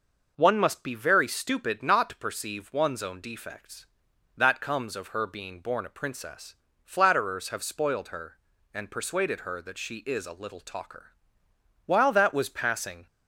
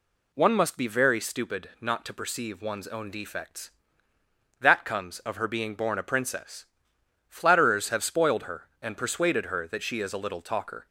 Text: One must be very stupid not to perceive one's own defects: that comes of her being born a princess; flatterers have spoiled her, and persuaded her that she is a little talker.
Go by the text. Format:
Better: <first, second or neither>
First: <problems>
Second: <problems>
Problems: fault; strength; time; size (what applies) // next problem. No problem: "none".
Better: second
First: goes on to say "While that was passing"; noticeable; from 11.8 s on; 1.2 s long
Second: none